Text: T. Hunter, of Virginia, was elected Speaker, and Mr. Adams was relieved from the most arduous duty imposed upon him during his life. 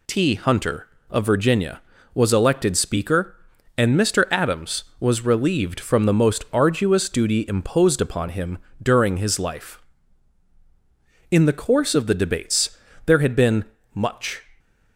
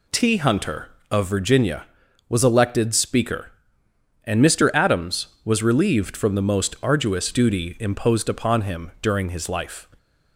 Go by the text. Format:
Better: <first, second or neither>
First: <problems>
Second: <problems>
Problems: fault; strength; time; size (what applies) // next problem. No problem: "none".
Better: second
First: pauses between "him" and "during"; slight; at 8.5 s; 0.24 s long // goes on to say "In the course of the debates there had been much"; strong; from 11.2 s on; 3.1 s long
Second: none